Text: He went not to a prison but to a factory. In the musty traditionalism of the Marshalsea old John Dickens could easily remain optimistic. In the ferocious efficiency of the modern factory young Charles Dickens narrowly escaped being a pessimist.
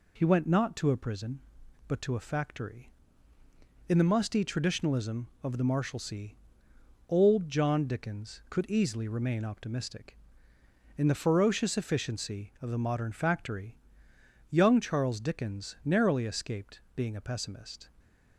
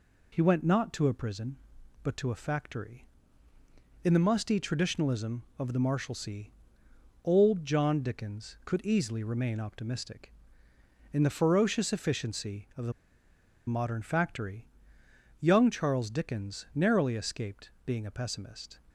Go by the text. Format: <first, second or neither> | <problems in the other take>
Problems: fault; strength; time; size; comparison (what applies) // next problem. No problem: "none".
first | pauses between "Marshalsea" and "old"; noticeable; at 6.4 s; 0.78 s long; noticeable in the first // pauses between "the" and "modern"; noticeable; at 12.9 s; 0.77 s long // pauses between "factory" and "young"; noticeable; at 14.6 s; 0.72 s long; noticeable in the first // pauses between "escaped" and "being"; slight; at 17.6 s; 0.16 s long; slight in the first